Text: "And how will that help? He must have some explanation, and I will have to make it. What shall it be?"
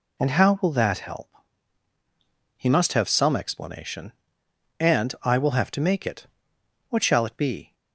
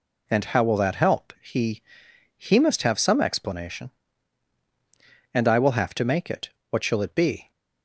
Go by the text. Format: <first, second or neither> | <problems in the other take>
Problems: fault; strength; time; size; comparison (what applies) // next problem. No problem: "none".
first | says "He" twice; at 2.3 s